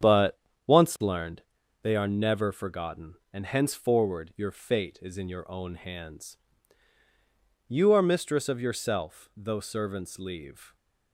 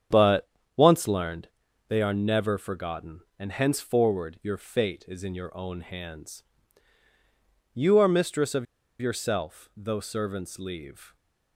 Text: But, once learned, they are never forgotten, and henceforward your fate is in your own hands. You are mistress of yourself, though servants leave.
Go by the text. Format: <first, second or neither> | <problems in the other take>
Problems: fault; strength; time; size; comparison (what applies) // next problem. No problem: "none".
first | starts louder than the rest; strong; until 1.3 s; 8 dB; strong in the first // pauses between "of" and "yourself"; at 8.6 s; 0.36 s long